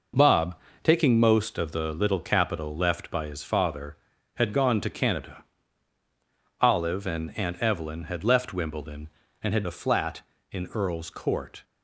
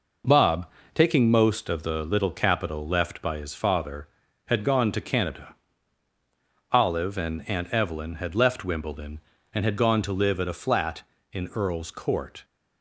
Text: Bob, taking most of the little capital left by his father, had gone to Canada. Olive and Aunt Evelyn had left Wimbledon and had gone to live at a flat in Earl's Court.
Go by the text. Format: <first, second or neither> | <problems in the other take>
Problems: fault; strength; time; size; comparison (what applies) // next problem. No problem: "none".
second | skips "gone to live at"; at 9.6 s